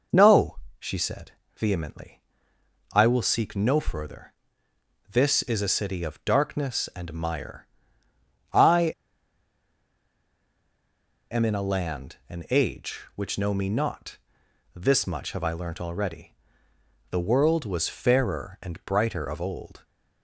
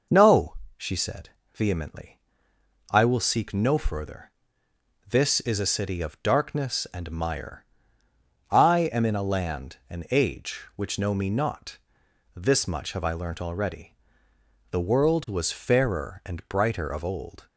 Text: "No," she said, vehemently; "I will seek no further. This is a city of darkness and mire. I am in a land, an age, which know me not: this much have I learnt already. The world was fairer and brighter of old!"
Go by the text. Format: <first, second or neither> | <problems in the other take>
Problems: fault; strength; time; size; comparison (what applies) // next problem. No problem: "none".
second | pauses between "I" and "am"; strong; at 8.9 s; 2.3 s long